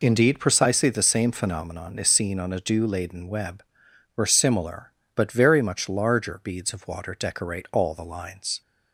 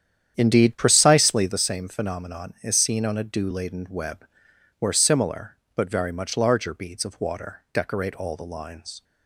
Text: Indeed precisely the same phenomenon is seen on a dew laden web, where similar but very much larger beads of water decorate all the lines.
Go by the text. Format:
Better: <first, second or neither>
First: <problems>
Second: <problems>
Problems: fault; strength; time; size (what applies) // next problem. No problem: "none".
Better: first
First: none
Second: starts louder than the rest; strong; until 1.7 s; 9 dB